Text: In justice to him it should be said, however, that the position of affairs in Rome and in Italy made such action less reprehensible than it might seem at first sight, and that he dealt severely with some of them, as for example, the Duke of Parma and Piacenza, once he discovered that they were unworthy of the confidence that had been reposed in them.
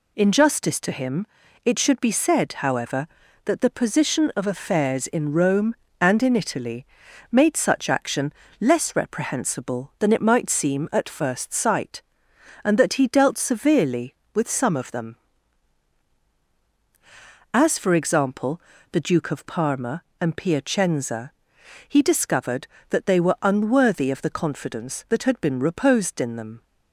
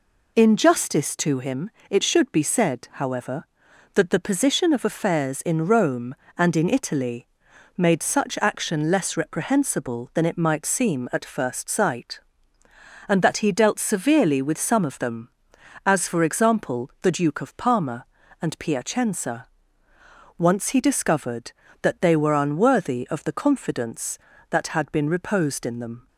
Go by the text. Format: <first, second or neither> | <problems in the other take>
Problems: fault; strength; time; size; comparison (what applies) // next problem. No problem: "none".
second | pauses between "him" and "it"; at 1.2 s; 0.38 s long; slight in the second // pauses between "Italy" and "made"; noticeable; at 6.8 s; 0.46 s long; noticeable in the second // pauses between "action" and "less"; slight; at 8.3 s; 0.26 s long // skips "once"; at 21.6 s